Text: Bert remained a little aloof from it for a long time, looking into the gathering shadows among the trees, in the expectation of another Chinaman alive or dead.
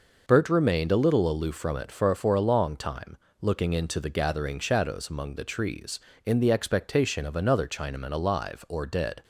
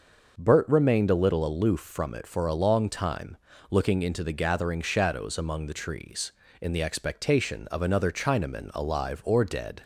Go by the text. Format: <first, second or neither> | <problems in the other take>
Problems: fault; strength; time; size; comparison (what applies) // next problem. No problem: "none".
second | says "for" twice; at 2.1 s